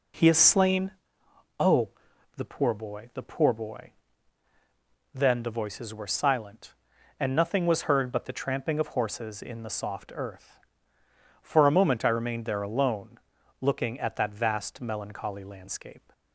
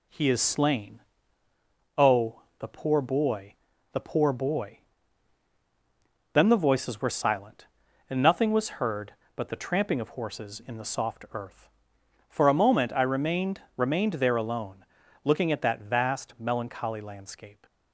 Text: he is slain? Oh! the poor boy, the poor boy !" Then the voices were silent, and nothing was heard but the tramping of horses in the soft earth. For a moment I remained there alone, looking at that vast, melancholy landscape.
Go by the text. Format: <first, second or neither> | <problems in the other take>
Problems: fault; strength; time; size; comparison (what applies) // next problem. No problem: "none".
first | says "remained" twice; at 13.7 s